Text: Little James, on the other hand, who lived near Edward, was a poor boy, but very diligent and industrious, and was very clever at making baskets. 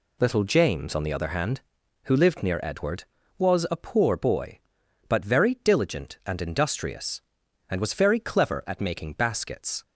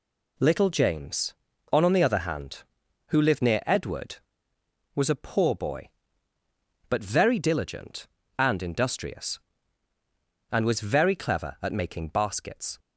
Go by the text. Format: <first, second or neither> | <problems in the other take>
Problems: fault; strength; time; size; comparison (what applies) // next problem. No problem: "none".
first | says "on" twice; at 1.8 s